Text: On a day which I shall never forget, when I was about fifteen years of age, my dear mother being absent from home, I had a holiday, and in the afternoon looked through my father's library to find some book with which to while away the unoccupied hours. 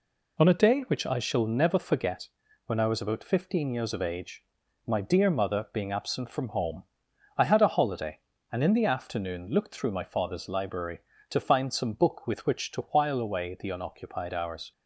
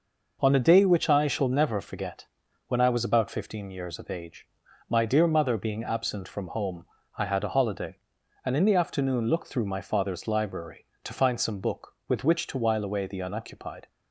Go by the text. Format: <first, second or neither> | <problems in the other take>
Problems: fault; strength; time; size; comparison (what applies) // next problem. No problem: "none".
first | stops before "hours"; at 13.8 s